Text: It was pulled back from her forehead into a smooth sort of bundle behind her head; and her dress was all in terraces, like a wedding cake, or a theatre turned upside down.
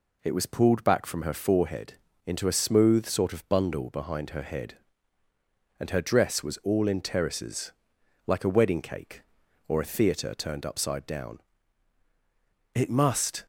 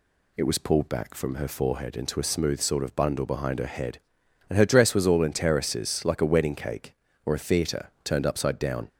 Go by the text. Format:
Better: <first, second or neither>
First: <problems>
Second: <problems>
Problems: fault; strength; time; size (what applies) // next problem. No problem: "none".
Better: second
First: pauses between "forehead" and "into"; slight; at 1.9 s; 0.32 s long // goes on to say "It must"; noticeable; from 12.7 s on; 0.70 s long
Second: none